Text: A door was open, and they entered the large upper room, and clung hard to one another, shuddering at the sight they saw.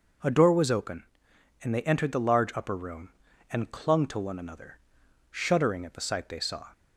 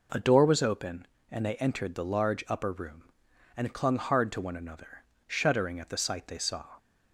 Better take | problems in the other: second | skips "hard"; at 4.0 s

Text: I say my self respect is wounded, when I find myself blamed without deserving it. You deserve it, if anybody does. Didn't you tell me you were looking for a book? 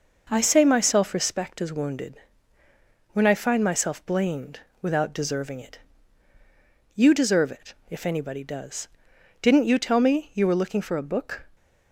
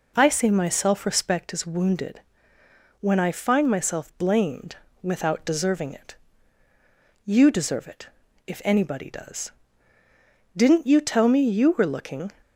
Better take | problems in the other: first | pauses between "blamed" and "without"; slight; at 4.7 s; 0.26 s long; slight in the first // stops before "for a book"; at 12.4 s

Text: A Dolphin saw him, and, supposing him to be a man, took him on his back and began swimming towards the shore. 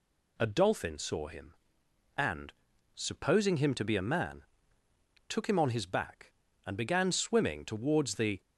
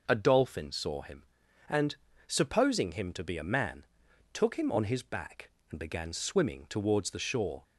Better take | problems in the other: second | stops before "shore"; at 8.4 s

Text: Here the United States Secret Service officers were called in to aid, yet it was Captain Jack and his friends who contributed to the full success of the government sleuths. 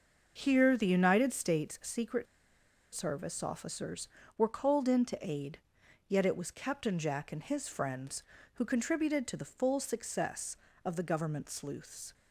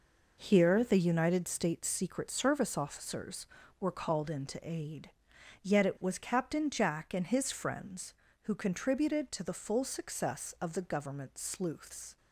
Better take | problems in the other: second | starts louder than the rest; noticeable; until 1.3 s; 6 dB // pauses between "Secret" and "Service"; noticeable; at 2.2 s; 0.69 s long

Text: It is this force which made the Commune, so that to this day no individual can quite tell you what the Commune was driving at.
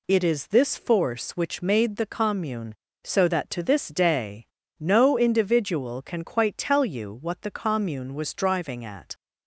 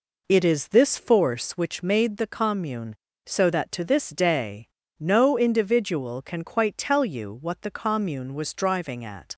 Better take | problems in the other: first | starts louder than the rest; noticeable; until 1.6 s; 4 dB // pauses between "day" and "no"; slight; at 4.6 s; 0.32 s long; slight in the first

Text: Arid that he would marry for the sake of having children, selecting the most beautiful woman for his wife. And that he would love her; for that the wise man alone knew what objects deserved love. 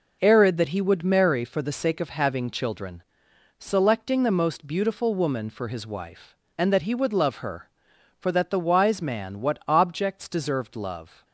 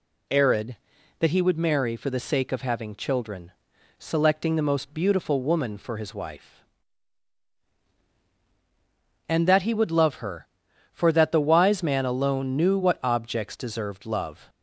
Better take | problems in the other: second | skips "alone knew"; at 9.4 s

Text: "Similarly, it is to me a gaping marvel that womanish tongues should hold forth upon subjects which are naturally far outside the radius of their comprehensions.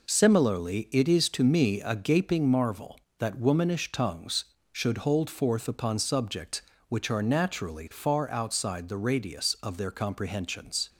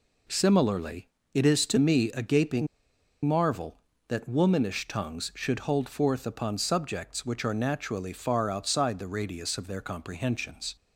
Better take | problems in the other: first | pauses between "gaping" and "marvel"; noticeable; at 2.6 s; 0.58 s long

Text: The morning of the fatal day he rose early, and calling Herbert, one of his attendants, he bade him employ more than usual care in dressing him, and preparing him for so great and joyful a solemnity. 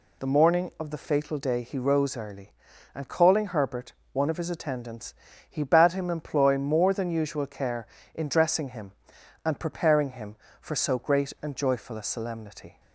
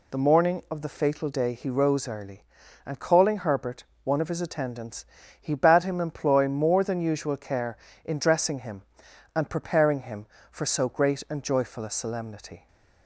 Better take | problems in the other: neither | none

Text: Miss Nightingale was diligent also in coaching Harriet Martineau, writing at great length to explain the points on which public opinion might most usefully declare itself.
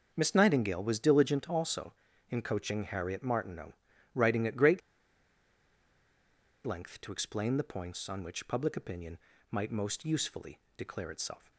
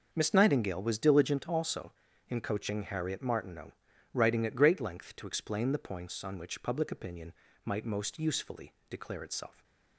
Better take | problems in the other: second | pauses between "great" and "length"; strong; at 4.8 s; 1.8 s long // pauses between "opinion" and "might"; slight; at 9.1 s; 0.34 s long; slight in the second // pauses between "usefully" and "declare"; slight; at 10.5 s; 0.18 s long; slight in the second

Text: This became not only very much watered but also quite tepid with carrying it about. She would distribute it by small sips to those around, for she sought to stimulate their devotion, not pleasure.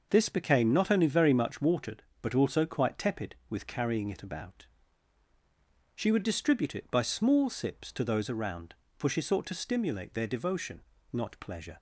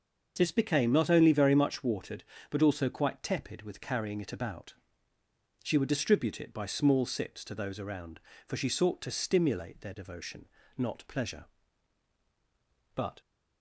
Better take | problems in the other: first | starts louder than the rest; until 1.3 s; 6 dB; noticeable in the first // goes on to say "But"; slight; from 12.9 s on; 0.26 s long

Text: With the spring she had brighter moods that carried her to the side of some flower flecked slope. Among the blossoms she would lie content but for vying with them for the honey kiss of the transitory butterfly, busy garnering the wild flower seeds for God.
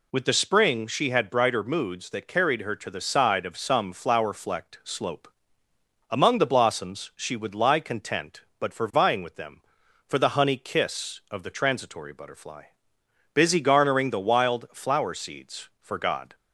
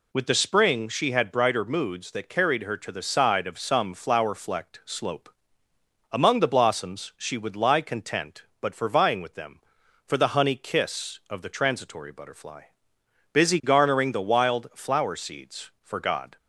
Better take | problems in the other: neither | none

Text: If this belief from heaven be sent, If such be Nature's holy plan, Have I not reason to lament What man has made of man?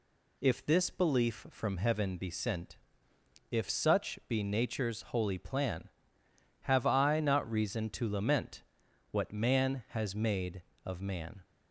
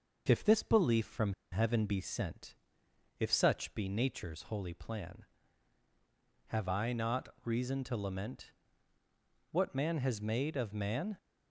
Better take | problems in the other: first | pauses between "from" and "heaven"; slight; at 1.3 s; 0.19 s long // pauses between "not" and "reason"; slight; at 7.2 s; 0.16 s long // pauses between "lament" and "What"; at 8.5 s; 1.0 s long; noticeable in the first

